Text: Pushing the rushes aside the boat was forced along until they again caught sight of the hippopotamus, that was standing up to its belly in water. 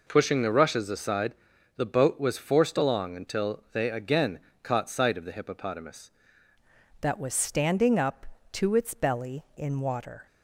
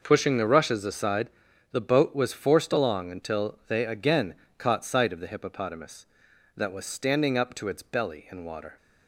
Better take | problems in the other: second | pauses between "aside" and "the"; at 1.3 s; 0.42 s long; also in the second // pauses between "again" and "caught"; slight; at 4.3 s; 0.24 s long; slight in the second // changes voice at "that"; from 7.0 s on; 3.2 s long

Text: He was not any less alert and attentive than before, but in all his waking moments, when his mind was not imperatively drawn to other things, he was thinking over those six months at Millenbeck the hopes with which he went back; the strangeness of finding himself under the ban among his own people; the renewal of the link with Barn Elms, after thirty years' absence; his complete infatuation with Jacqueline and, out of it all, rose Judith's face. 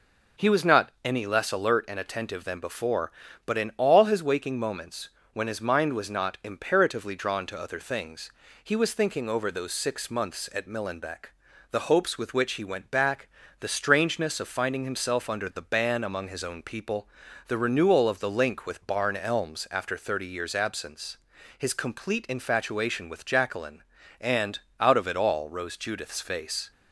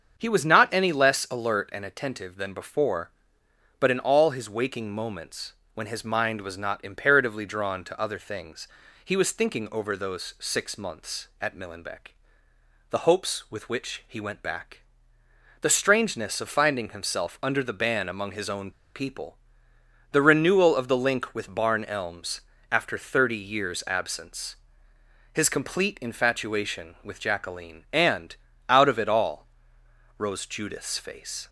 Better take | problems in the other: first | starts louder than the rest; until 1.1 s; 7 dB // pauses between "Millenbeck" and "the"; noticeable; at 12.1 s; 0.76 s long; also in the first // pauses between "own" and "people"; slight; at 18.7 s; 0.24 s long

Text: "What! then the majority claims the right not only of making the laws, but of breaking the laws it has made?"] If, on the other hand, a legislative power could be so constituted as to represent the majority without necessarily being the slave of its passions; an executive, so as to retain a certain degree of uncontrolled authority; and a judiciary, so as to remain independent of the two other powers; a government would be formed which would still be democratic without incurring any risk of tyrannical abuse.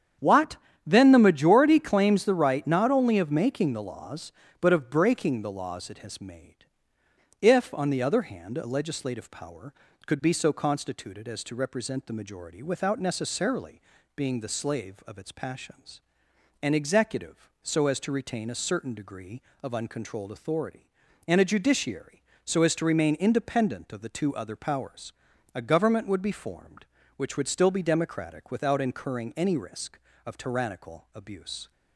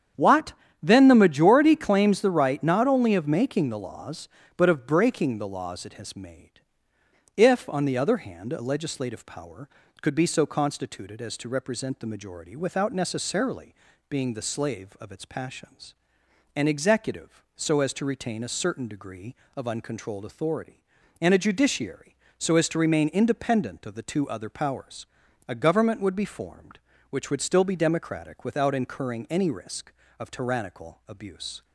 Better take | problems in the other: neither | starts louder than the rest; strong; the same in both // pauses between "necessarily" and "being"; slight; the same in both

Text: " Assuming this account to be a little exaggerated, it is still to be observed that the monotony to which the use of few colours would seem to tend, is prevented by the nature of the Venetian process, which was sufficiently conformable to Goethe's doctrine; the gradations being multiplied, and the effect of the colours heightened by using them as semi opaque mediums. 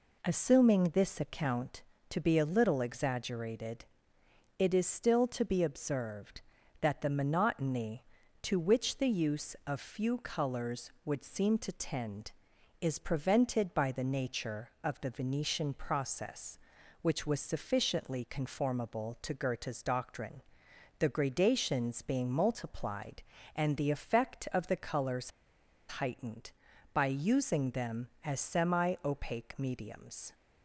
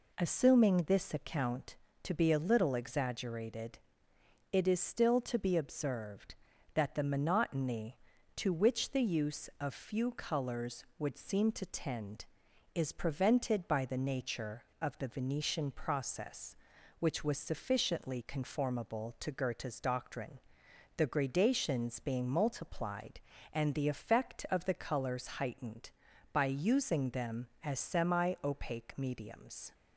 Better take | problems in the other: second | pauses between "colours" and "heightened"; noticeable; at 25.2 s; 0.68 s long

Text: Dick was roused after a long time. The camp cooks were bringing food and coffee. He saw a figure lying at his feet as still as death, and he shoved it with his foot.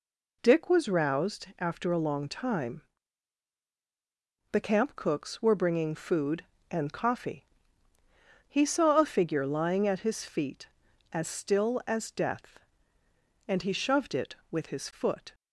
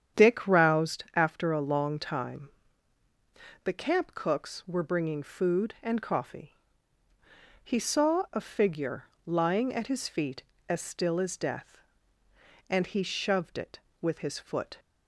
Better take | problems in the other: first | starts louder than the rest; strong; until 1.2 s; 8.5 dB // skips "was"; at 0.4 s // pauses between "figure" and "lying"; slight; at 9.0 s; 0.22 s long

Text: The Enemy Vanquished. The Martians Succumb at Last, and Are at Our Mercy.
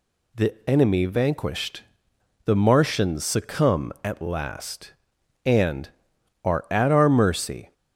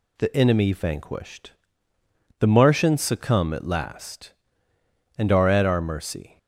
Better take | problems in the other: neither | none

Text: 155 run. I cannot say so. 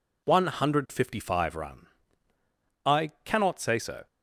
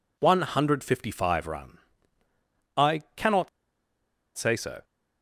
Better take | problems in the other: first | pauses between "cannot" and "say"; noticeable; at 3.4 s; 0.88 s long

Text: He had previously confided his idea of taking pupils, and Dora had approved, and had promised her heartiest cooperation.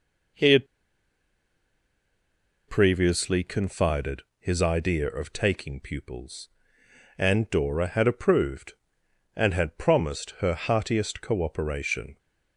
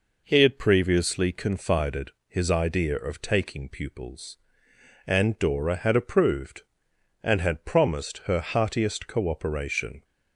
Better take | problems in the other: second | pauses between "had" and "previously"; strong; at 0.6 s; 2.0 s long // pauses between "confided" and "his"; slight; at 4.2 s; 0.16 s long; slight in the second

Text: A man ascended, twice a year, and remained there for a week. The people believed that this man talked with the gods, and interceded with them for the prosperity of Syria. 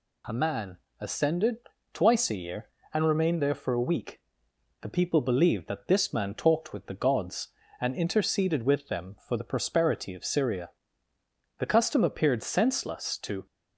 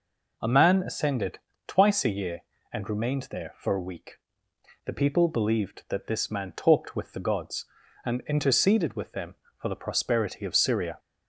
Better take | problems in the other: second | pauses between "man" and "ascended"; slight; at 0.7 s; 0.22 s long // goes on to say "The custom appeared senseless to"; strong; from 11.5 s on; 1.8 s long

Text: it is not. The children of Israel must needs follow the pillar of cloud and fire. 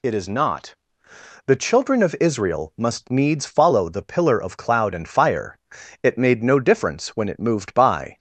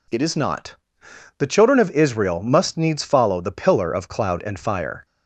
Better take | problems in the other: second | goes on to say "It made no difference when it moved by"; strong; from 6.0 s on; 2.1 s long

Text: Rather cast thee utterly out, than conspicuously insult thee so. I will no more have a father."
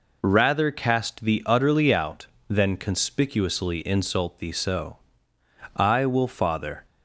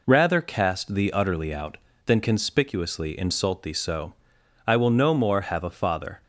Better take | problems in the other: second | skips "no more have a"; at 6.2 s

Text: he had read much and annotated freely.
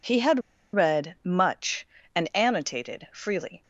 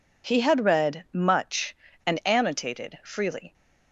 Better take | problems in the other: second | pauses between "had" and "read"; slight; at 0.3 s; 0.35 s long

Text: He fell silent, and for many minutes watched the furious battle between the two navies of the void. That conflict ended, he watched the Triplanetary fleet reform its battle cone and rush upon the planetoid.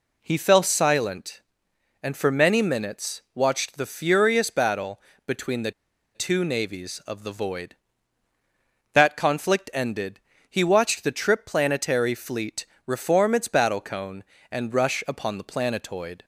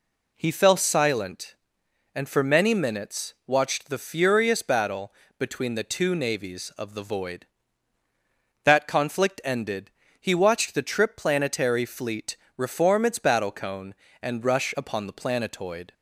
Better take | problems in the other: second | pauses between "battle" and "between"; slight; at 5.0 s; 0.26 s long; slight in the second // pauses between "the" and "two"; at 5.7 s; 0.43 s long // pauses between "fleet" and "reform"; slight; at 12.6 s; 0.20 s long; slight in the second

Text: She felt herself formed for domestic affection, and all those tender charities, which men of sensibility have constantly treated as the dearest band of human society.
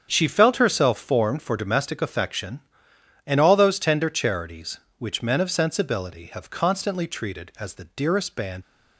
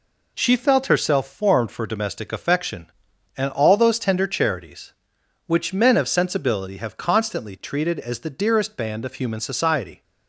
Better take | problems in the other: second | starts louder than the rest; strong; until 1.1 s; 7.5 dB // stops before "of human society"; at 8.6 s

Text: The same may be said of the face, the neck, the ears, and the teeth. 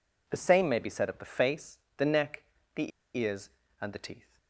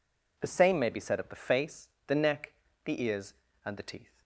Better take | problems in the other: second | pauses between "the" and "ears"; slight; at 2.9 s; 0.26 s long

